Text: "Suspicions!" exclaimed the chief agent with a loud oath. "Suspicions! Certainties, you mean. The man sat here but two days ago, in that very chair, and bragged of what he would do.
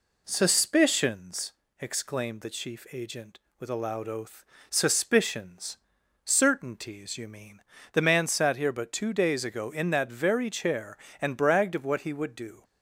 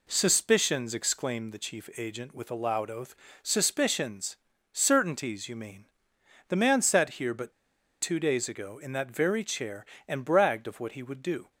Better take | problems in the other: first | pauses between "but" and "two"; noticeable; at 7.5 s; 0.49 s long

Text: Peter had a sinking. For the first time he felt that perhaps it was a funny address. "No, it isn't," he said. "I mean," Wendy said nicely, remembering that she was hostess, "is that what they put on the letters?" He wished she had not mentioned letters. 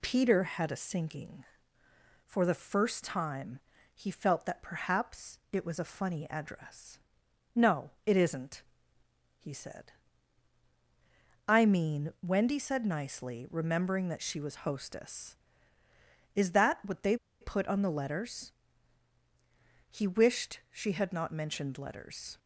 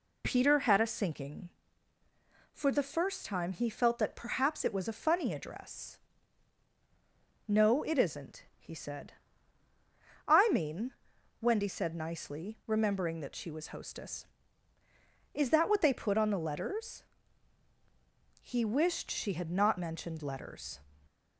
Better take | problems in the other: second | pauses between "time" and "he"; slight; at 3.5 s; 0.34 s long // pauses between "they" and "put"; slight; at 17.1 s; 0.25 s long

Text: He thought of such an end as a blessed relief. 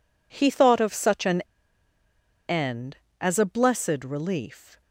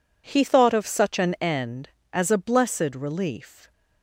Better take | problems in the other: second | pauses between "an" and "end"; at 1.4 s; 1.0 s long

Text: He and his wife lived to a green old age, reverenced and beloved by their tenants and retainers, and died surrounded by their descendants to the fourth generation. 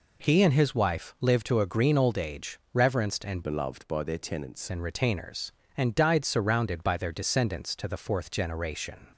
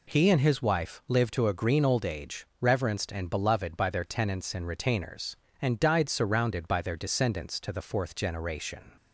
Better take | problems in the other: second | changes voice from "beloved" to "tenants"; from 3.4 to 4.6 s; 1.2 s long

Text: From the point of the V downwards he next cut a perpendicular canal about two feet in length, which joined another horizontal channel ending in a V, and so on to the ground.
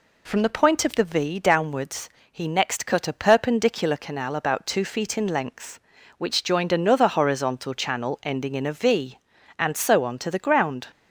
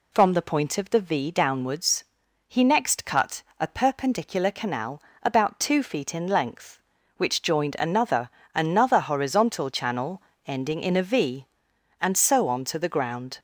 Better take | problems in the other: first | pauses between "downwards" and "he"; at 2.0 s; 0.42 s long; slight in the first // pauses between "cut" and "a"; slight; at 3.4 s; 0.16 s long // pauses between "canal" and "about"; slight; at 5.0 s; 0.20 s long // says "another" twice; at 8.5 s // pauses between "channel" and "ending"; slight; at 10.1 s; 0.24 s long

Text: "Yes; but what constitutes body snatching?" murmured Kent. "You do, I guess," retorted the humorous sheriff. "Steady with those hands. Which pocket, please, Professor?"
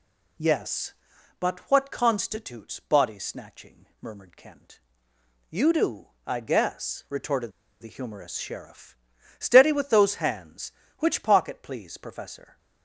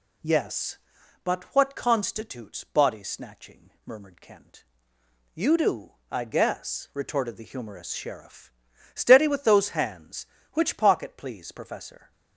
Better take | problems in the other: second | pauses between "retorted" and "the"; slight; at 7.5 s; 0.30 s long

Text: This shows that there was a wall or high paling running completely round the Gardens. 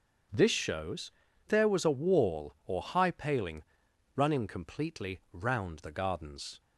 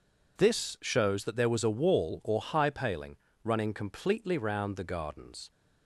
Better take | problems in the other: second | starts louder than the rest; strong; until 1.7 s; 7.5 dB // skips "that"; at 1.2 s // pauses between "paling" and "running"; noticeable; at 3.6 s; 0.52 s long; slight in the second

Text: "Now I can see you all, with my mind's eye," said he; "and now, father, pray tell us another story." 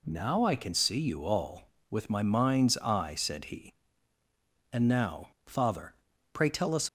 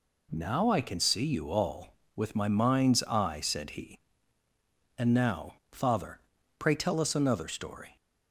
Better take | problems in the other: second | stops before "another story"; at 6.8 s

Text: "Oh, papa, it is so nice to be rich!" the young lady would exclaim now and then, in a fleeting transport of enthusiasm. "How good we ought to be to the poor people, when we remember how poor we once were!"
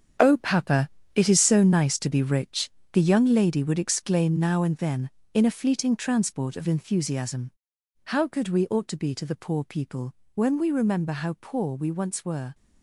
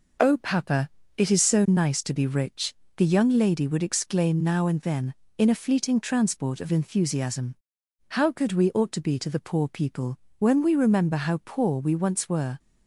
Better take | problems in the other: second | gets quieter; strong; throughout; 10 dB

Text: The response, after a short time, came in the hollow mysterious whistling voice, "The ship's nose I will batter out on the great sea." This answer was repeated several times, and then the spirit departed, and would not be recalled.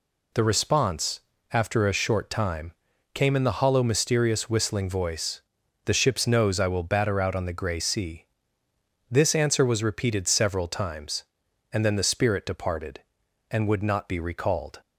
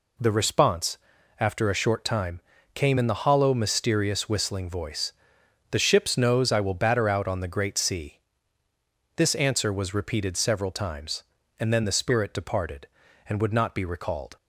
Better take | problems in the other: second | says "grey" for "great"; at 7.5 s

